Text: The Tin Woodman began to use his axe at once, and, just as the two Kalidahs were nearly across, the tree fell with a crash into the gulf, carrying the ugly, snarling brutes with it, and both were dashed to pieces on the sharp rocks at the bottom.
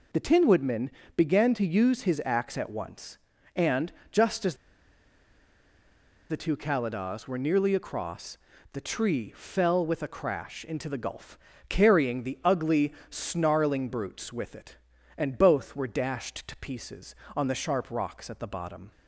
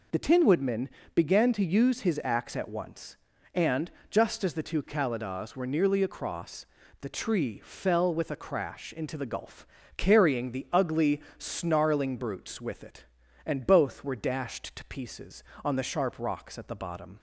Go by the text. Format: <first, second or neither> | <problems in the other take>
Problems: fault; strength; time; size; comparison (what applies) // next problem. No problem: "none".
second | pauses between "Woodman" and "began"; slight; at 0.8 s; 0.26 s long; slight in the second // pauses between "as" and "the"; strong; at 4.5 s; 1.7 s long